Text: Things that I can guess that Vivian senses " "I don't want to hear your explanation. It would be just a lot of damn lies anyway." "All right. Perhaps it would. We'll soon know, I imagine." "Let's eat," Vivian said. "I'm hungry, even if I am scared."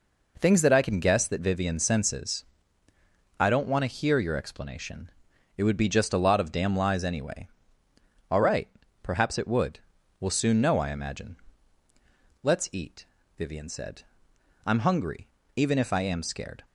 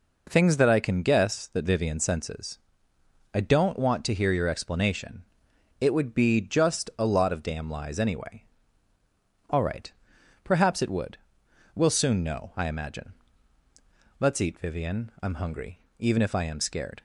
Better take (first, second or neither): first